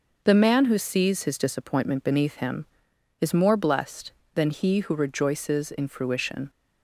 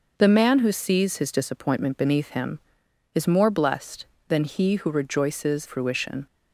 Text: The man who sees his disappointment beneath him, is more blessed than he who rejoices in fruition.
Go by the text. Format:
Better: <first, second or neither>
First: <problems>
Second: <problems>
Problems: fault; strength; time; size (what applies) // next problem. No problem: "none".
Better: first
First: none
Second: skips "in"; at 5.6 s